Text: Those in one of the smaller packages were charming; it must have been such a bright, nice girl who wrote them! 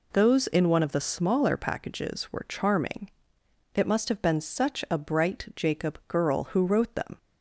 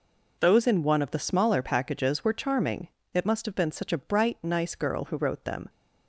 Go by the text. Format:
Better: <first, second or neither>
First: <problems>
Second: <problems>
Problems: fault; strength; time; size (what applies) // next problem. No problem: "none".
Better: second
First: says "jacob" for "nice"; at 5.5 s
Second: none